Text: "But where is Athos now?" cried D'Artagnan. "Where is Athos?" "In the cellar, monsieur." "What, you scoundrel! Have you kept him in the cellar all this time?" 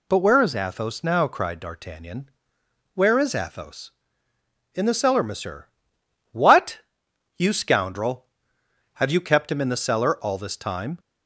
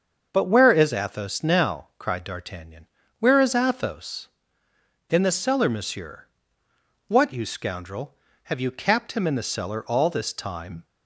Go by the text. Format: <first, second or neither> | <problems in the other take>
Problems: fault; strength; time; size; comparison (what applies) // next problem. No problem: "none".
first | starts louder than the rest; until 1.3 s; 6.5 dB // says "capped" for "kept"; at 8.7 s